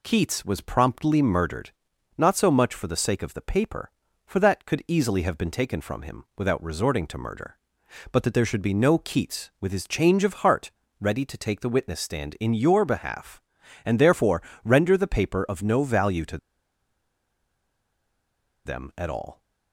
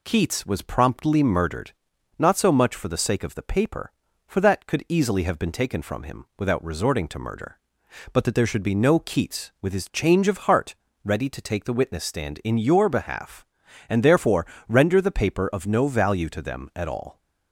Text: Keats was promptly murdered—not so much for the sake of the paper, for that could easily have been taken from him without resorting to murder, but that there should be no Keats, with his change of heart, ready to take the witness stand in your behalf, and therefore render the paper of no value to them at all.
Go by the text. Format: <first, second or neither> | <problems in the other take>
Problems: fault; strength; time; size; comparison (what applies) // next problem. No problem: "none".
second | pauses between "therefore" and "render"; slight; at 14.4 s; 0.22 s long; slight in the second // pauses between "to" and "them"; strong; at 16.3 s; 2.2 s long